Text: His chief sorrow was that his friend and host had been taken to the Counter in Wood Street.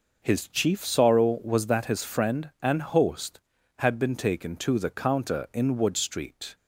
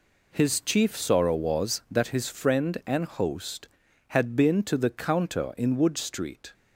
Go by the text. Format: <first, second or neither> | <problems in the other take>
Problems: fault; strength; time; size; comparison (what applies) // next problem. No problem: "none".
first | skips "taken"; at 4.6 s